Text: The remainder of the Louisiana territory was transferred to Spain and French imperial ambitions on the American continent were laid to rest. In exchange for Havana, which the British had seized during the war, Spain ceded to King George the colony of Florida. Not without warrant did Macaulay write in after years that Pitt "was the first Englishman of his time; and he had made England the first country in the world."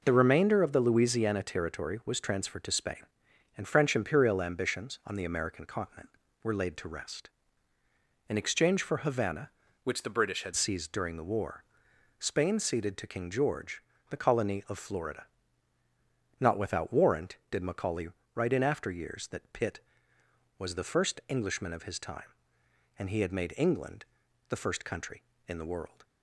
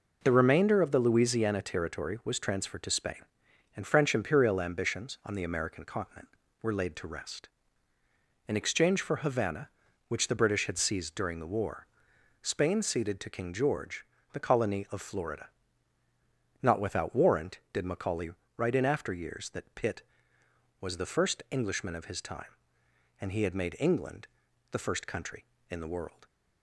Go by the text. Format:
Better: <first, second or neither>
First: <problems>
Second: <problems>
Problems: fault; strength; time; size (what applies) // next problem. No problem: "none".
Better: second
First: changes voice from "which" to "had"; from 9.8 to 10.5 s; 0.7 s long // pauses between "George" and "the"; slight; at 13.8 s; 0.28 s long // pauses between "Macaulay" and "write"; slight; at 18.0 s; 0.26 s long // pauses between "England" and "the"; at 24.0 s; 0.44 s long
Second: pauses between "George" and "the"; slight; at 14.0 s; 0.28 s long // pauses between "Macaulay" and "write"; slight; at 18.3 s; 0.26 s long // pauses between "England" and "the"; at 24.2 s; 0.44 s long